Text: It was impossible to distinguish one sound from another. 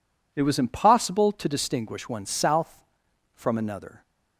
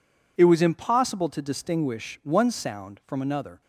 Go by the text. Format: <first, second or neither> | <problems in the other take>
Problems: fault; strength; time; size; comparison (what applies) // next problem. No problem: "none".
second | says "south" for "sound"; at 2.2 s